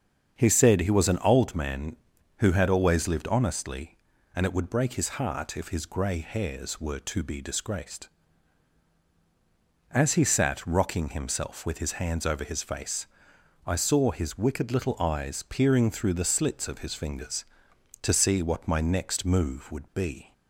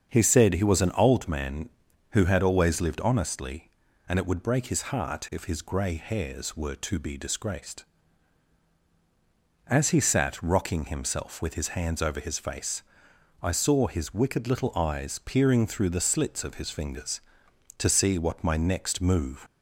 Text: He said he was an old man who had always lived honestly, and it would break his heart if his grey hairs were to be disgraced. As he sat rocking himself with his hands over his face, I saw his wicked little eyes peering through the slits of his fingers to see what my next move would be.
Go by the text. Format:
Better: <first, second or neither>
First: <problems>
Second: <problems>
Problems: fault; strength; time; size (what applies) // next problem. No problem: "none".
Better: first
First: starts louder than the rest; strong; until 1.4 s; 7.5 dB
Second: starts louder than the rest; strong; until 1.1 s; 7.5 dB // stops before "would be"; at 19.4 s